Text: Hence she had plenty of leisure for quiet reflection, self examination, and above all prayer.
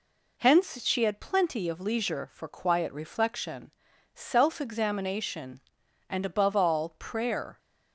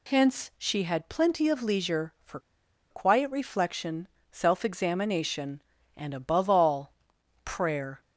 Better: first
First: none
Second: pauses between "for" and "quiet"; noticeable; at 2.3 s; 0.51 s long // pauses between "all" and "prayer"; noticeable; at 6.9 s; 0.50 s long

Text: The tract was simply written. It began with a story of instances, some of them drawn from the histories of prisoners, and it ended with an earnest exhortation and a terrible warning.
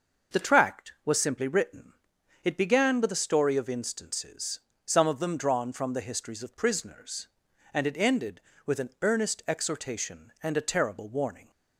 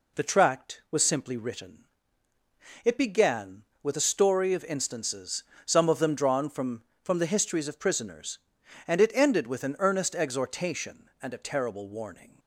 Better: first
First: none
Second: says "from" twice; at 7.0 s

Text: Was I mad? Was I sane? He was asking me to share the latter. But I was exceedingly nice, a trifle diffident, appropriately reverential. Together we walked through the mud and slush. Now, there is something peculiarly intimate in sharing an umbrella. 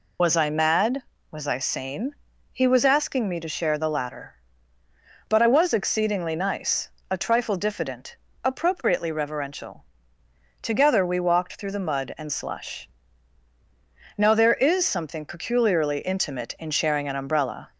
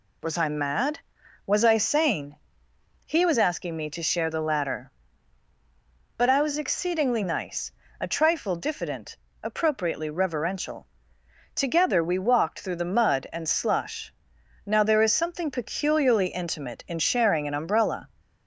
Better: second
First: loses the start of "Was"; at 0.1 s; 45 ms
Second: none

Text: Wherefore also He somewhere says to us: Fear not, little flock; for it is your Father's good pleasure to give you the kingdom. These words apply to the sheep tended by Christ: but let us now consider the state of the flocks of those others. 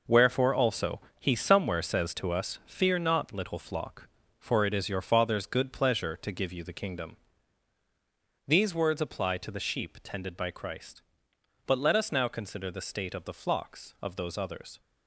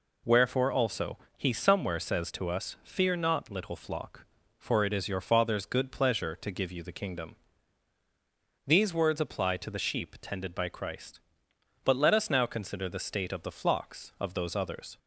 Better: second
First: gets quieter; strong; throughout; 9 dB // pauses between "also" and "He"; slight; at 0.9 s; 0.20 s long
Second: pauses between "also" and "He"; slight; at 1.1 s; 0.20 s long

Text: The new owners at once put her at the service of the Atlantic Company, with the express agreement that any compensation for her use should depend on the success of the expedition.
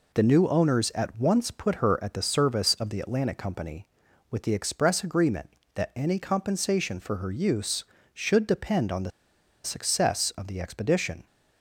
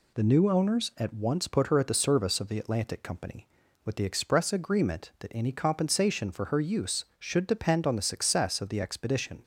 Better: second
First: pauses between "the" and "success"; noticeable; at 9.1 s; 0.53 s long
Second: none

